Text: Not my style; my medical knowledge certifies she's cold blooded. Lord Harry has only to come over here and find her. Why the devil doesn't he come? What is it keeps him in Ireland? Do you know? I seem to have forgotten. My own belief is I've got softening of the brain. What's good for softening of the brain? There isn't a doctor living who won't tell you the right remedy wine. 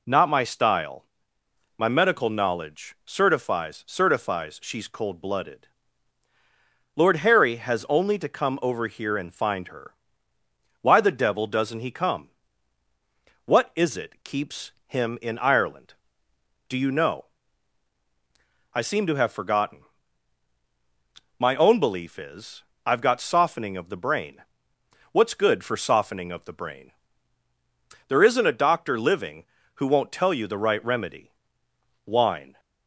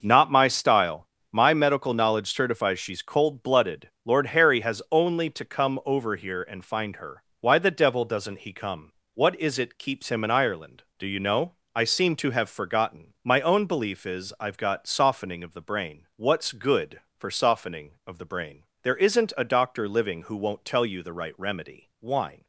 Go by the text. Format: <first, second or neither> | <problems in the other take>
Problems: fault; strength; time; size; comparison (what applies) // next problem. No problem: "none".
second | says "certifies" twice; at 3.8 s // pauses between "keeps" and "him"; slight; at 14.7 s; 0.16 s long // pauses between "is" and "I've"; slight; at 22.6 s; 0.22 s long // pauses between "remedy" and "wine"; noticeable; at 31.3 s; 0.74 s long